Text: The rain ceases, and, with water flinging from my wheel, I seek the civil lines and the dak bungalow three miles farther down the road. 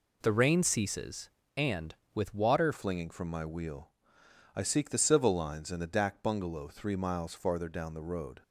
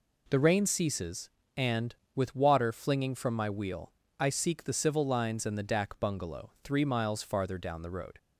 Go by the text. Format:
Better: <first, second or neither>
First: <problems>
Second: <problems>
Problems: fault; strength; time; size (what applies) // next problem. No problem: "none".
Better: second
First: changes voice at "flinging"; from 2.7 s on; 5.7 s long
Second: none